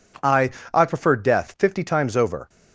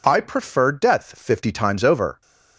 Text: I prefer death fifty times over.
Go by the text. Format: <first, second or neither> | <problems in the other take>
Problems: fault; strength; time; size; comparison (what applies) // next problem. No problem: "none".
second | says "I" twice; at 0.7 s